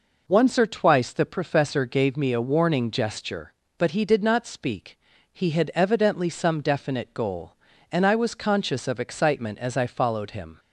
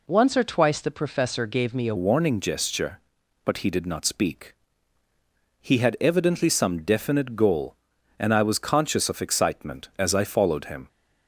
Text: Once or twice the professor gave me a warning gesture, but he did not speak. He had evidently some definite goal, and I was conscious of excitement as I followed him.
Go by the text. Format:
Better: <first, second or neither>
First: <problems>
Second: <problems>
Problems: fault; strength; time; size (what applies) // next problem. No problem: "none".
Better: first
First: none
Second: changes voice at "warning"; from 1.9 s on; 8.9 s long